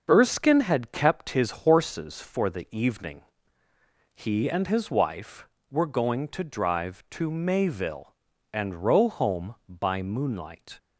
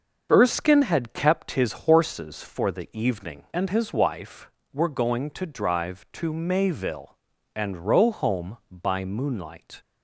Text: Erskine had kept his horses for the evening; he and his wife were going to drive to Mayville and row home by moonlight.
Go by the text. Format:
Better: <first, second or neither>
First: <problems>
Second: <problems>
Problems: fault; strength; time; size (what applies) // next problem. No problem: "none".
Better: first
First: starts louder than the rest; until 1.0 s; 6 dB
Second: starts louder than the rest; until 1.3 s; 6.5 dB // skips "he"; at 3.4 s